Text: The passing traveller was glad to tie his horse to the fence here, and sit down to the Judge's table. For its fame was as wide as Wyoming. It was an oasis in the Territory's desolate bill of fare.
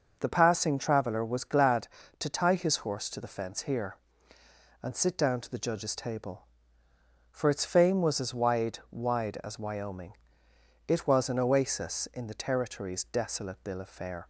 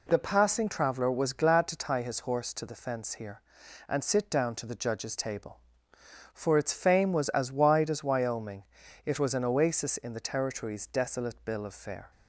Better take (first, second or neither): second